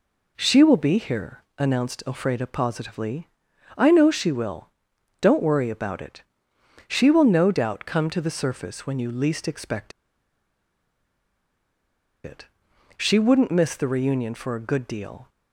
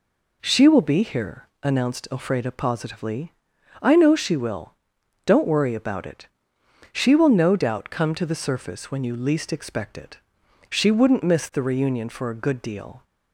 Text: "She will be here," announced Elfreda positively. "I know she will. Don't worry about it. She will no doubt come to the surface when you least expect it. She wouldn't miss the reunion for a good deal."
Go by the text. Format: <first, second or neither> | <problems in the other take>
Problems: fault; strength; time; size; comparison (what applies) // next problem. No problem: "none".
second | pauses between "expect" and "it"; strong; at 9.9 s; 2.3 s long